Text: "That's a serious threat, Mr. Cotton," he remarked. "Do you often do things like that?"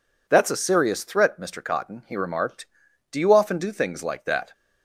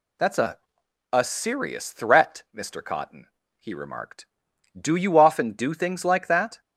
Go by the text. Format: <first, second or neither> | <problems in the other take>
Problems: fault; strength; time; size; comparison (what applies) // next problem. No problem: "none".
first | says "a" twice; at 1.1 s